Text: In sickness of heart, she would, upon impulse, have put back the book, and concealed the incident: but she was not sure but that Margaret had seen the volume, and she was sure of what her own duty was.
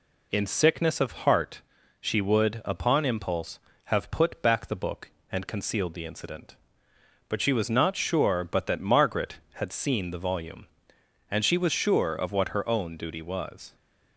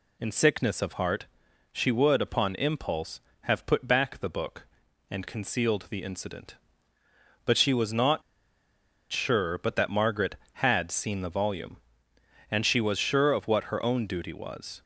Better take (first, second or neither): first